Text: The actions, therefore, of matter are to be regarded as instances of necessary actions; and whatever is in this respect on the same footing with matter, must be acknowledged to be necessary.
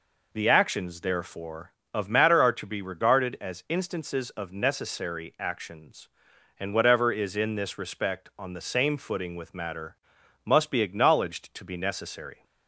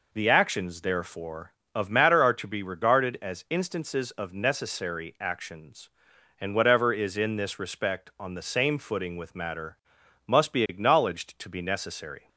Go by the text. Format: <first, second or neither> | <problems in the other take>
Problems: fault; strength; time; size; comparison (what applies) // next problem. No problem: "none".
neither | none